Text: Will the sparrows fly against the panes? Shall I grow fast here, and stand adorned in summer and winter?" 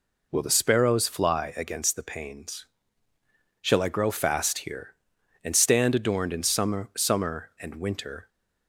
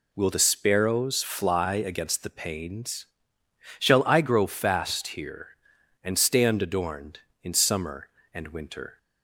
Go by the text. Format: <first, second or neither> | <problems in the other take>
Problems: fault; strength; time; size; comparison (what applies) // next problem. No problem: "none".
second | says "summer" twice; at 6.9 s